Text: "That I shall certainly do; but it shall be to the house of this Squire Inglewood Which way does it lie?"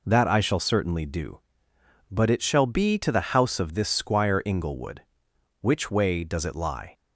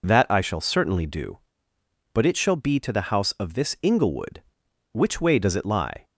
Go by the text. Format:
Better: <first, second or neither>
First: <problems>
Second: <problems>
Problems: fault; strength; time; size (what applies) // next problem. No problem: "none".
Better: first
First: none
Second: skips "Squire"; at 3.7 s